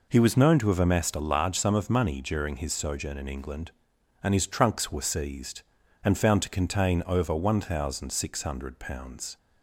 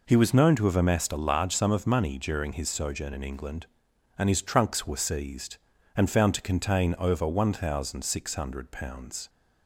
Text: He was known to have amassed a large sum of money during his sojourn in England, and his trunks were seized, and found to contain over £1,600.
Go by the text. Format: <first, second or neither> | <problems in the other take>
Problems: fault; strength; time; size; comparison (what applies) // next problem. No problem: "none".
neither | none